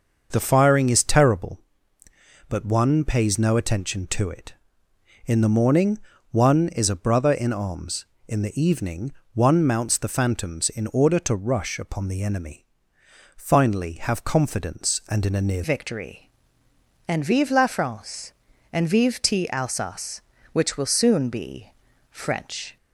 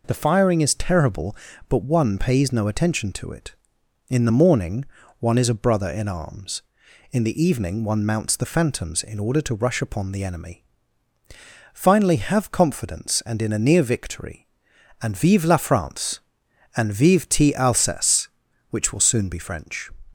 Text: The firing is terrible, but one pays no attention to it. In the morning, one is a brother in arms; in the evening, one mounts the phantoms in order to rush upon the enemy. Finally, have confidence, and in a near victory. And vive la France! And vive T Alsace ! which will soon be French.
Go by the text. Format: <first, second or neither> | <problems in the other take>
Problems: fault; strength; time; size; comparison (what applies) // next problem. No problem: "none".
second | starts louder than the rest; until 1.3 s; 6 dB // changes voice at "victory"; from 15.6 s on; 7.1 s long // pauses between "be" and "French"; at 21.6 s; 0.42 s long